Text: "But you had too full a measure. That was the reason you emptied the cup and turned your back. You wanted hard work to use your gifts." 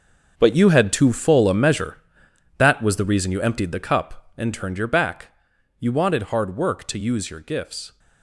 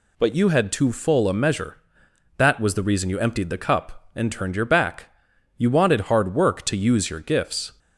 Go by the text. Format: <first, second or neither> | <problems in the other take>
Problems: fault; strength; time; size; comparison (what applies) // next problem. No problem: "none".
second | gets quieter; strong; throughout; 11.5 dB